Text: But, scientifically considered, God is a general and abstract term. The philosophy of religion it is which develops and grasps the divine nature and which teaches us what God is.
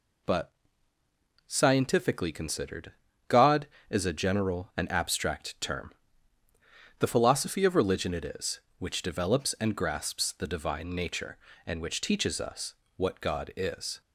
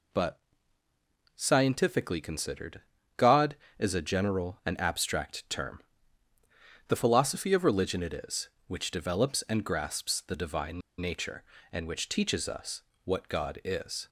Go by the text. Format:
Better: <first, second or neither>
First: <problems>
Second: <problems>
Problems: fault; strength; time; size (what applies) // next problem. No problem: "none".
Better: first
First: pauses between "us" and "what"; slight; at 12.7 s; 0.22 s long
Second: pauses between "divine" and "nature"; slight; at 10.8 s; 0.19 s long // pauses between "us" and "what"; slight; at 12.8 s; 0.22 s long